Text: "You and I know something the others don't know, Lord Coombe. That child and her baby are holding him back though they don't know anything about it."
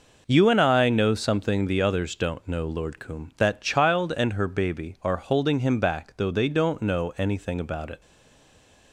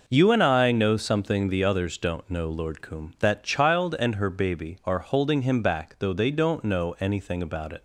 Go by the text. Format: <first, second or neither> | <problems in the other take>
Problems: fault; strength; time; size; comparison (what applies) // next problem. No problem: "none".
second | stays silent after the last word; slight; from 8.0 s on; 0.9 s long